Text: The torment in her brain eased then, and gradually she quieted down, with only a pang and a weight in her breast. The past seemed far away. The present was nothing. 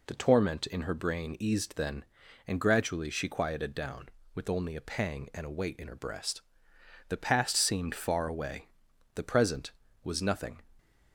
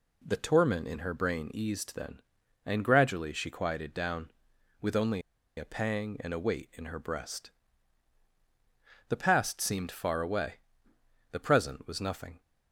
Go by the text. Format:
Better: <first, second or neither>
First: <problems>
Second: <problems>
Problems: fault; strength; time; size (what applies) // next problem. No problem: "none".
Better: first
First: none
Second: pauses between "only" and "a"; at 5.2 s; 0.36 s long